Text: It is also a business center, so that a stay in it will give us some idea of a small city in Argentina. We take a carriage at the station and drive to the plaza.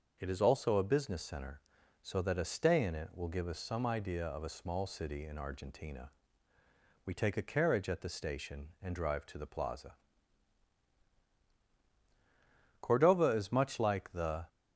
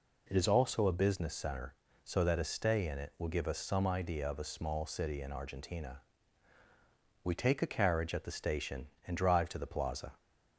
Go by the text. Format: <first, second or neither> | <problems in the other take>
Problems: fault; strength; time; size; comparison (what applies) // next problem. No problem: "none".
second | starts louder than the rest; until 1.2 s; 6 dB // goes on to say "Cordova is much like the"; strong; from 12.7 s on; 1.6 s long